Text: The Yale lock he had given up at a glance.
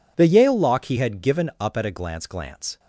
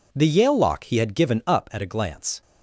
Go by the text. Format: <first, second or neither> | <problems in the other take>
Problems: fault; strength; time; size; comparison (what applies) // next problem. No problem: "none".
second | says "glance" twice; at 2.2 s